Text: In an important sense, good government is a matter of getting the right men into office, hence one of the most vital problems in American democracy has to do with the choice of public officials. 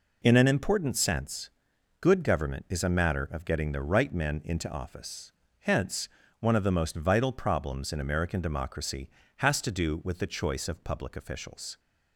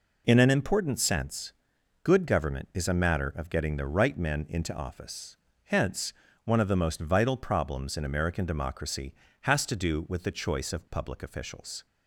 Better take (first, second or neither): neither